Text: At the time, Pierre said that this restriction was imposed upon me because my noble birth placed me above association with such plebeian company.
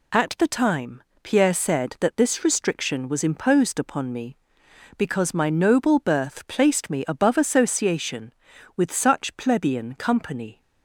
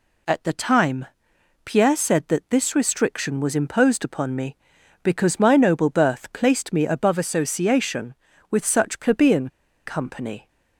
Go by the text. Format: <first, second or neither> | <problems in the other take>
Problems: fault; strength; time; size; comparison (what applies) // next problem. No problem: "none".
first | pauses between "plebeian" and "company"; at 9.4 s; 0.36 s long